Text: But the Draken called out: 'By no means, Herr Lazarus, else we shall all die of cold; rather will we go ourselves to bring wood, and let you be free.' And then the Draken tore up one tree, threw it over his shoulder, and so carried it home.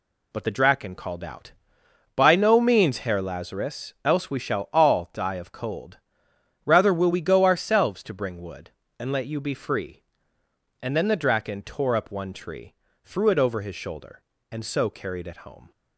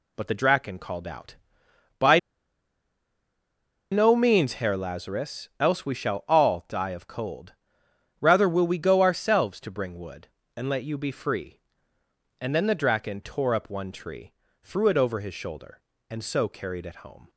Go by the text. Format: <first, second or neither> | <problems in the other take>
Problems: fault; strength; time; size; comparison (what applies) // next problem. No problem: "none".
first | pauses between "By" and "no"; strong; at 2.1 s; 1.7 s long